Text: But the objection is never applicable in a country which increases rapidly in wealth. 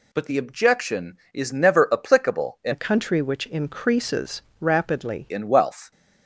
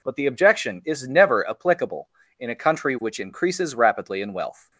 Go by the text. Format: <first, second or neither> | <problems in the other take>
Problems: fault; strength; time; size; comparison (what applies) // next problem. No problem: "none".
second | changes voice from "a" to "rapidly"; from 2.7 to 5.2 s; 2.5 s long // pauses between "increases" and "rapidly"; slight; at 4.4 s; 0.18 s long